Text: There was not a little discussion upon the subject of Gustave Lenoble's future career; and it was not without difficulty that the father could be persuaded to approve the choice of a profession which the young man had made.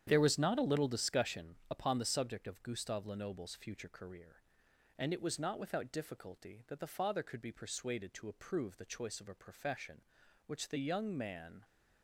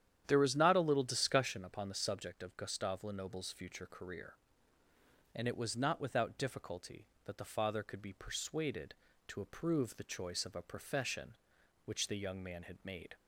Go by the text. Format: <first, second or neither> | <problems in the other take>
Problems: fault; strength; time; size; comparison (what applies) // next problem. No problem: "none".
second | starts louder than the rest; strong; until 1.0 s; 9.5 dB; strong in the second // stops before "had made"; at 11.6 s